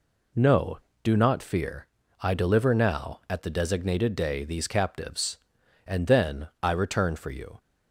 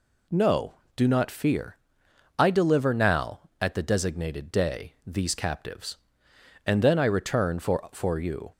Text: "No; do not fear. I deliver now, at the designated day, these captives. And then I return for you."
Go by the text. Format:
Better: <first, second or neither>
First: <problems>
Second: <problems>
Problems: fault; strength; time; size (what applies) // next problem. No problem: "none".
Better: first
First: none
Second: says "for" twice; at 7.9 s